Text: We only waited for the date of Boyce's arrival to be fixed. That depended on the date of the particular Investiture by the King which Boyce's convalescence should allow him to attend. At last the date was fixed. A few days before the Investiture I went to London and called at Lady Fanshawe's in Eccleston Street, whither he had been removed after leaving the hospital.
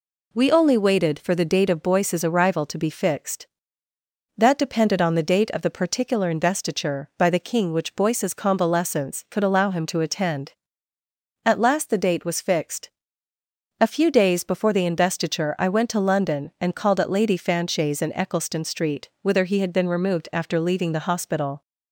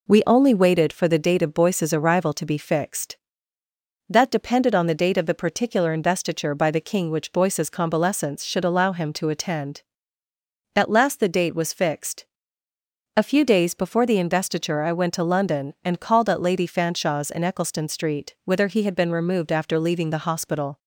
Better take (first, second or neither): second